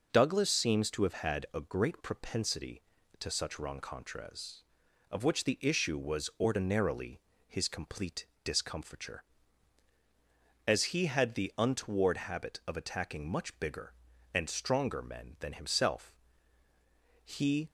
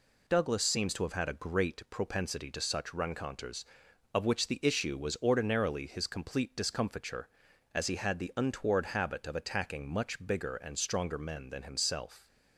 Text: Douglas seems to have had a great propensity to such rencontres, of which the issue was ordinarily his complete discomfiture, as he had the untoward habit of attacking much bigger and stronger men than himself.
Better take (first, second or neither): second